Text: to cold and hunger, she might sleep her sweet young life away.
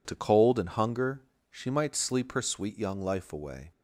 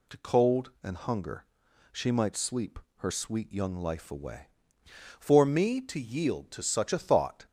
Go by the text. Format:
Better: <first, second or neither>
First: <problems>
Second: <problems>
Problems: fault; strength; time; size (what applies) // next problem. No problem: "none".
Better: first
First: none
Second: pauses between "sleep" and "her"; slight; at 2.7 s; 0.18 s long // goes on to say "For me to yield to such a thought"; strong; from 5.1 s on; 2.2 s long